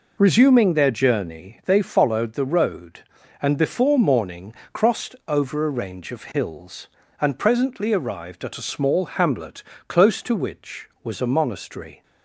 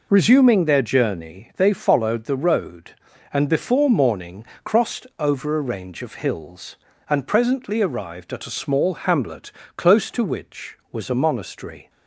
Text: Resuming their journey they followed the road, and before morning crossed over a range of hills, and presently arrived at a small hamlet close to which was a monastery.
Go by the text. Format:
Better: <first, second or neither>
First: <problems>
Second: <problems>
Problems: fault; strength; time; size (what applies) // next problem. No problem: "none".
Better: neither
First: pauses between "morning" and "crossed"; slight; at 4.5 s; 0.20 s long // pauses between "hamlet" and "close"; slight; at 9.6 s; 0.26 s long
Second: pauses between "morning" and "crossed"; slight; at 4.4 s; 0.20 s long // pauses between "hamlet" and "close"; slight; at 9.5 s; 0.26 s long